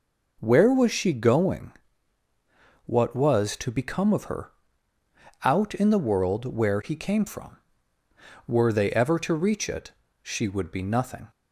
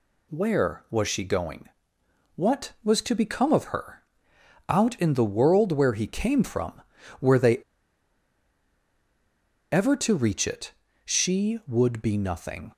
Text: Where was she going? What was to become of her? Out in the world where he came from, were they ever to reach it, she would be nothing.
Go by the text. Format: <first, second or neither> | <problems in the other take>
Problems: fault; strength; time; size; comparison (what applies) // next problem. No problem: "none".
first | pauses between "they" and "ever"; strong; at 7.5 s; 2.1 s long